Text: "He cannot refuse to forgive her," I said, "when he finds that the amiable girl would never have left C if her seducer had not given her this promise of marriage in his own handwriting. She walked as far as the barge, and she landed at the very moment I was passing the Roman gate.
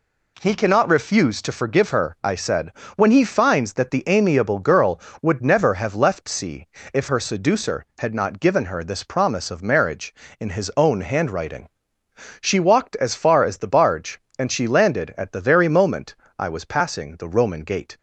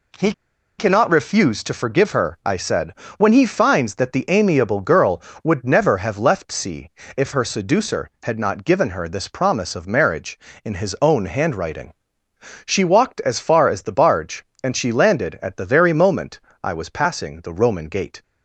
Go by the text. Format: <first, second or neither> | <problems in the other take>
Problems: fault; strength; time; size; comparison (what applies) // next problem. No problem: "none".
first | pauses between "He" and "cannot"; at 0.3 s; 0.44 s long // pauses between "C" and "if"; slight; at 6.8 s; 0.24 s long; slight in the first // pauses between "moment" and "I"; slight; at 16.3 s; 0.24 s long; slight in the first